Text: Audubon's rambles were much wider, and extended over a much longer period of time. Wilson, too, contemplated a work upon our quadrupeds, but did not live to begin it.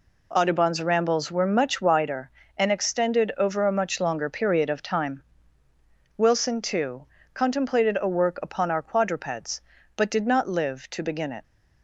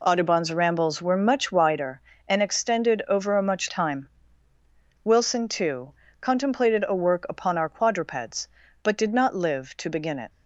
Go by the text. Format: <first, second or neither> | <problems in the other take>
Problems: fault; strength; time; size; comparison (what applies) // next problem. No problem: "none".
first | skips "longer period of"; at 3.6 s